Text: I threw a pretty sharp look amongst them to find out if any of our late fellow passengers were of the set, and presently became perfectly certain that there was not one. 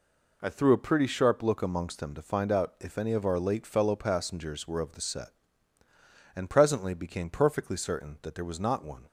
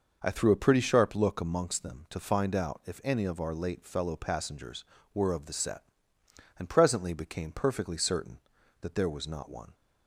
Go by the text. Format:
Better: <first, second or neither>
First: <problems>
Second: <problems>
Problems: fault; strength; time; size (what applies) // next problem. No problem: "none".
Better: neither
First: none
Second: none